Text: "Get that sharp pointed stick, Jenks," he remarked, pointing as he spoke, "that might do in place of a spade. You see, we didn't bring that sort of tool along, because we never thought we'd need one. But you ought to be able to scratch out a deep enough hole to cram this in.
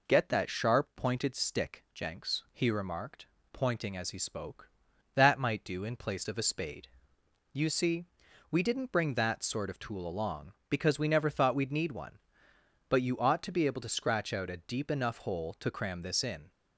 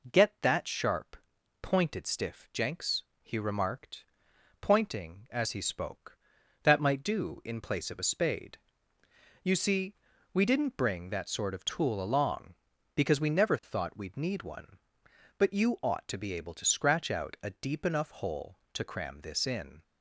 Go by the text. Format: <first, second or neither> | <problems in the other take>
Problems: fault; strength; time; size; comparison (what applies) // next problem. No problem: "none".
first | pauses between "sharp" and "pointed"; noticeable; at 1.1 s; 0.48 s long // says "stiff" for "stick"; at 2.0 s